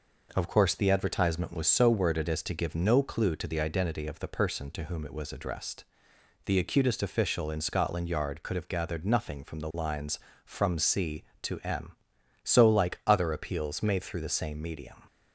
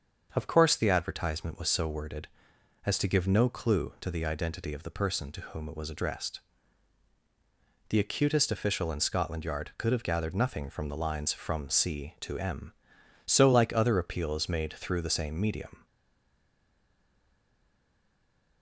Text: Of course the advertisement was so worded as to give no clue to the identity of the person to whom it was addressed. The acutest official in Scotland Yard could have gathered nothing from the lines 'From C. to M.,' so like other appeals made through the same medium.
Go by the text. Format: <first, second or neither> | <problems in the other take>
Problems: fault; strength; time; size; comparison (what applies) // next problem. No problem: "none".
first | starts louder than the rest; until 1.3 s; 6.5 dB // stays silent after the last word; strong; from 15.8 s on; 2.8 s long